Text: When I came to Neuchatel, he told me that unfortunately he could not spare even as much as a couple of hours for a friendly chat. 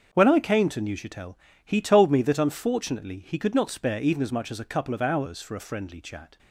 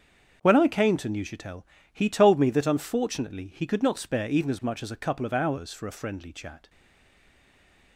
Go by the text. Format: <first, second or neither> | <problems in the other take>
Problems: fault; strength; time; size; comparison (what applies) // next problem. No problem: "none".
first | starts louder than the rest; until 1.4 s; 7 dB; also in the first // stays silent after the last word; noticeable; from 6.6 s on; 1.3 s long